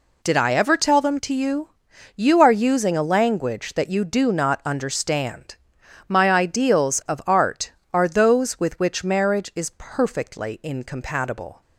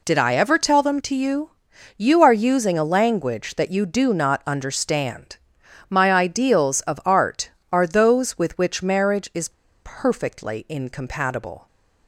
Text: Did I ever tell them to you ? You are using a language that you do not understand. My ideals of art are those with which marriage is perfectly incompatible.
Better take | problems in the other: first | pauses between "is" and "perfectly"; slight; at 9.5 s; 0.31 s long

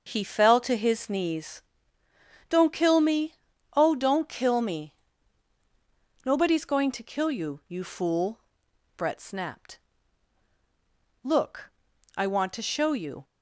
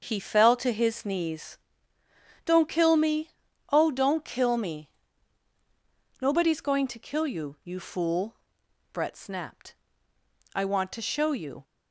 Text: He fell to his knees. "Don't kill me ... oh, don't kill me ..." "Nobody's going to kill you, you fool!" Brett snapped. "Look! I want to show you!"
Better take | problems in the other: first | starts louder than the rest; until 1.0 s; 6.5 dB; also in the first // skips "Look"; at 10.1 s

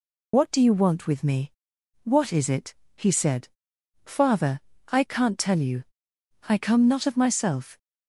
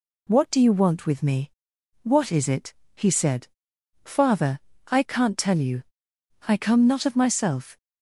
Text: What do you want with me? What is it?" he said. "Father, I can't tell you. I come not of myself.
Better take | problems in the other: second | loses the start of "What"; at 0.3 s; 40 ms

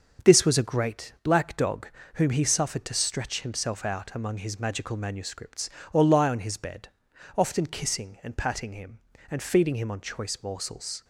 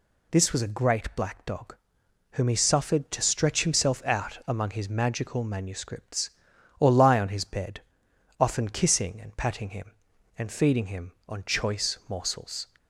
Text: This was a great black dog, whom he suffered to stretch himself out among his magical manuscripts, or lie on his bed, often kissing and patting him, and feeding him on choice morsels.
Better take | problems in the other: second | gets quieter; noticeable; throughout; 6 dB

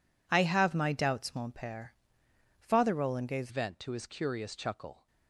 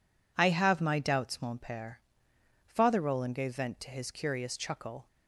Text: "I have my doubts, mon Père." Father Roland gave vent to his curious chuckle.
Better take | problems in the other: second | changes voice at "vent"; from 3.4 s on; 1.6 s long

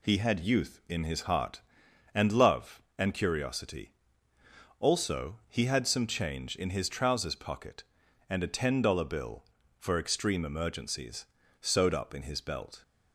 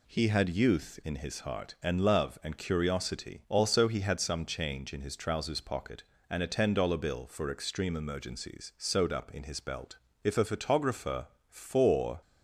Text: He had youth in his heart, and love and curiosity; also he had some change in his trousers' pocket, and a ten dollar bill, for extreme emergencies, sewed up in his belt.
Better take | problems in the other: first | goes on to say "If a photographer for"; strong; from 10.2 s on; 1.9 s long

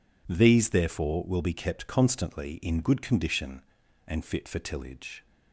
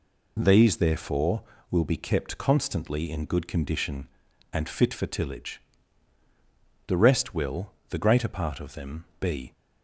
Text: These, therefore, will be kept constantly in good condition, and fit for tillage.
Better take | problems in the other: first | goes on to say "The rest will the greater part of them be"; strong; from 6.8 s on; 2.6 s long

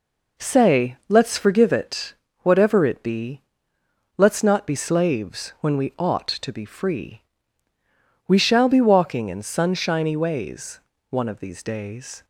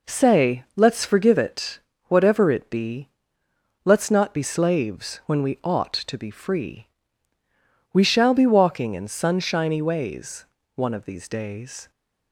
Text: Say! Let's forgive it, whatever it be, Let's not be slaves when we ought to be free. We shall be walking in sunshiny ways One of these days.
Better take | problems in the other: neither | pauses between "ways" and "One"; slight; the same in both

